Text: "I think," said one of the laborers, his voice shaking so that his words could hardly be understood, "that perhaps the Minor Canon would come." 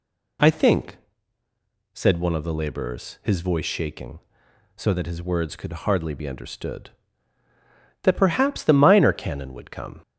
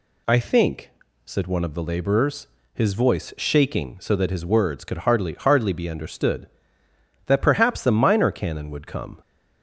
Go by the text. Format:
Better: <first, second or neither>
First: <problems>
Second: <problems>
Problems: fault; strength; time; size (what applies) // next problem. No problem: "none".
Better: first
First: none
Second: says "hardly" twice; at 5.3 s